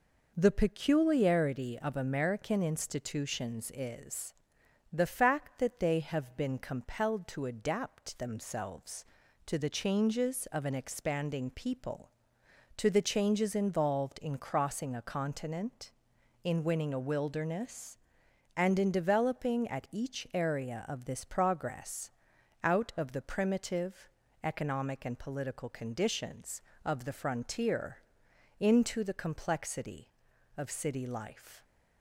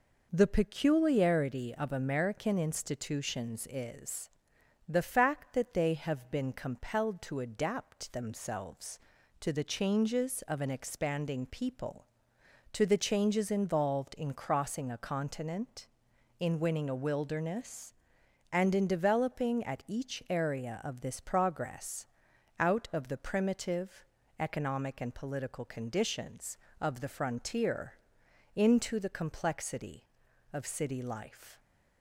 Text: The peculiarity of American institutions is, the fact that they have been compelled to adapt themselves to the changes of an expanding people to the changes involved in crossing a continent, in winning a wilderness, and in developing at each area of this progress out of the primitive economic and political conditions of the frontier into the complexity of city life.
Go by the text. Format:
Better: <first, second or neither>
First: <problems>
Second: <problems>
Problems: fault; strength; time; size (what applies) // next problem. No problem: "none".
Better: neither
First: pauses between "progress" and "out"; noticeable; at 22.0 s; 0.54 s long // pauses between "primitive" and "economic"; slight; at 24.0 s; 0.34 s long // pauses between "frontier" and "into"; noticeable; at 27.9 s; 0.62 s long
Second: pauses between "progress" and "out"; noticeable; at 22.0 s; 0.54 s long // pauses between "primitive" and "economic"; slight; at 24.0 s; 0.34 s long // pauses between "frontier" and "into"; noticeable; at 27.9 s; 0.62 s long